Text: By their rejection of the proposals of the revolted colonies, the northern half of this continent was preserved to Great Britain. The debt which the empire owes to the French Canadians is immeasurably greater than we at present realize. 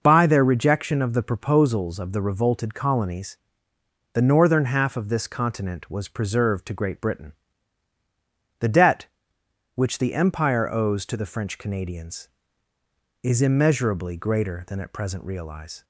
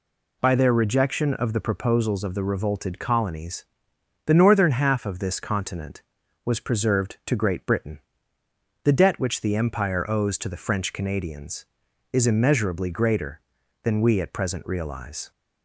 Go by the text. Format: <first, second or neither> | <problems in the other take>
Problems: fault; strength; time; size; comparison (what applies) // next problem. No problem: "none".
second | skips "we"; at 14.7 s